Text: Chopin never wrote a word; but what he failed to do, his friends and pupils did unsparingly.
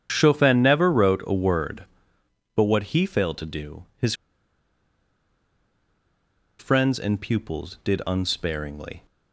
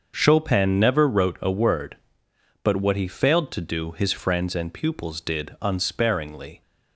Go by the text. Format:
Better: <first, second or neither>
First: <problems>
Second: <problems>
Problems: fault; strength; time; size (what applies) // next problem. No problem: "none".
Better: second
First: starts louder than the rest; strong; until 1.1 s; 8.5 dB // pauses between "his" and "friends"; strong; at 4.1 s; 2.4 s long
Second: starts louder than the rest; until 1.1 s; 6.5 dB